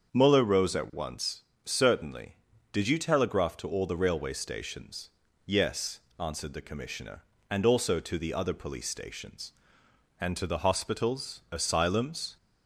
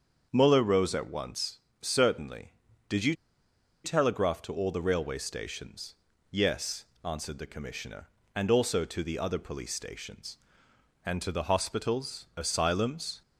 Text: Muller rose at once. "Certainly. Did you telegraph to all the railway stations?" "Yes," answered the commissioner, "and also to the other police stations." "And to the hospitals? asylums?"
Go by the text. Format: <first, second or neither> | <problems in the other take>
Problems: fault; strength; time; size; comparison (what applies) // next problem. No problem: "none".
first | starts louder than the rest; until 1.3 s; 7 dB; also in the first // pauses between "you" and "telegraph"; noticeable; at 3.1 s; 0.69 s long